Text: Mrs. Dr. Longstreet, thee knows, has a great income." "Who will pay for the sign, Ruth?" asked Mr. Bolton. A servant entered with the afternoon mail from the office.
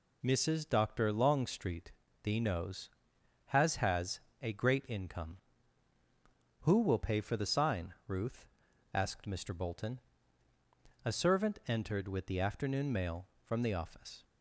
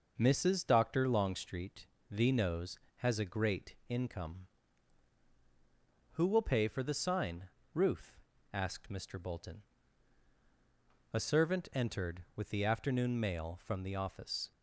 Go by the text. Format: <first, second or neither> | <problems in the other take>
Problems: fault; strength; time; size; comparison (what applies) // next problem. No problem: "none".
second | says "has" twice; at 3.7 s